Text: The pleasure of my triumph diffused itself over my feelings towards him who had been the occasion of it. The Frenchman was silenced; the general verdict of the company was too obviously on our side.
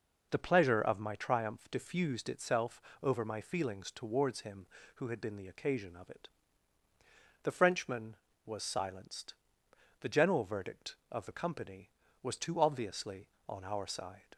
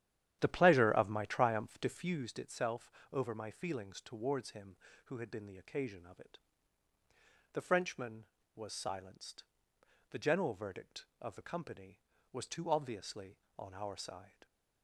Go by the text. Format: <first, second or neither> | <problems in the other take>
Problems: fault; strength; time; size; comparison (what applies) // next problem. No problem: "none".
first | starts louder than the rest; strong; until 2.1 s; 11 dB // pauses between "itself" and "over"; slight; at 2.9 s; 0.20 s long; slight in the first